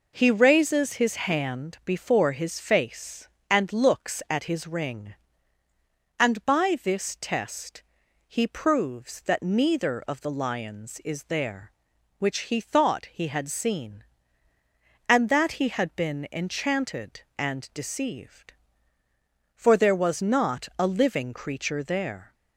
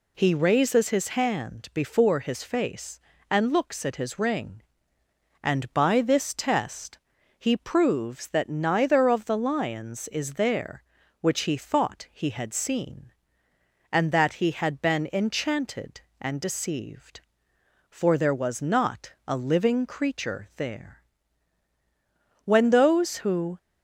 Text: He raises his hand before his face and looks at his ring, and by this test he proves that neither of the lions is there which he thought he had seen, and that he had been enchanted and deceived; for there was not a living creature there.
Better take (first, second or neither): first